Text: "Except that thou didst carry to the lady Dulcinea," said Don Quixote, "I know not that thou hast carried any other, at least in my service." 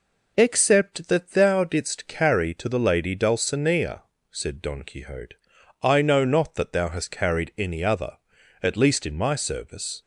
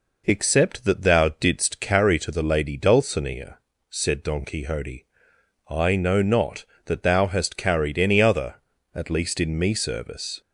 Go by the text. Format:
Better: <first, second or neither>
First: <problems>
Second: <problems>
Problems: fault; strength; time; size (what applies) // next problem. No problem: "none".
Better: first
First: none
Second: says "me" for "my"; at 9.5 s